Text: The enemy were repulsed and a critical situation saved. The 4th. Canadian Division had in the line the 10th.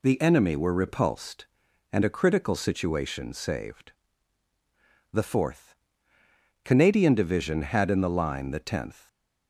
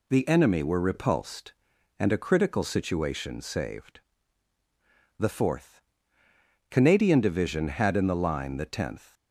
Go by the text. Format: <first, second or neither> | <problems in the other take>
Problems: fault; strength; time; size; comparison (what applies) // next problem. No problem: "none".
neither | none